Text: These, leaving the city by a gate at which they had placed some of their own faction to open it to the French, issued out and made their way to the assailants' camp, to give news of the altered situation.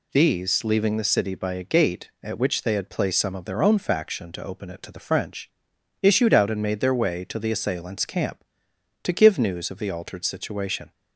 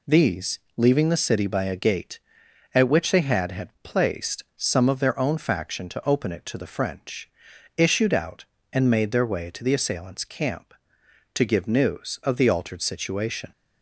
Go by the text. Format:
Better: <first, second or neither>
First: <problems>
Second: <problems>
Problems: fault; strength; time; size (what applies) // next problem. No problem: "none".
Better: first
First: none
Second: says "had" twice; at 3.5 s